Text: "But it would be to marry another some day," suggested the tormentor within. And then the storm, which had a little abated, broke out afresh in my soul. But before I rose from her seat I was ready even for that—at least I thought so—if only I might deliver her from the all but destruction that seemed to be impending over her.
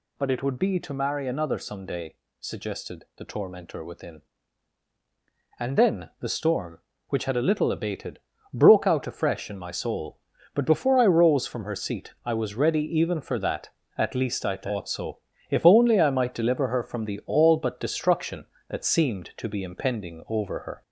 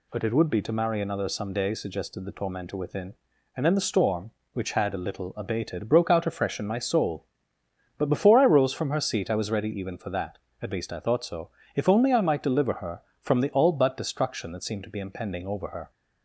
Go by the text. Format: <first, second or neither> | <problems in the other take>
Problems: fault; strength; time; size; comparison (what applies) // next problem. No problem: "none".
second | gets louder; slight; throughout; 2 dB // pauses between "ready" and "even"; slight; at 12.8 s; 0.16 s long